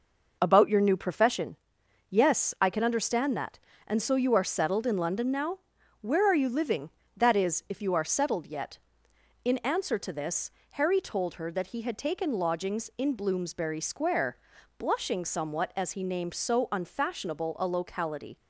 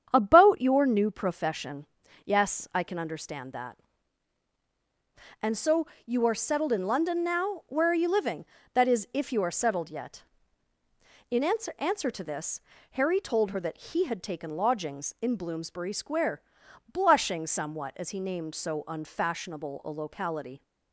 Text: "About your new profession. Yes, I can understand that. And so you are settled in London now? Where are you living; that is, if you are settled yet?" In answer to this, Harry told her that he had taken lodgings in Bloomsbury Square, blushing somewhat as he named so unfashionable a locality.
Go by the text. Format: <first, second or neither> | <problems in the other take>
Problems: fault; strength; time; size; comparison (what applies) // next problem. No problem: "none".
first | starts louder than the rest; strong; until 1.1 s; 8 dB // pauses between "so" and "you"; slight; at 5.8 s; 0.22 s long // says "answer" twice; at 11.7 s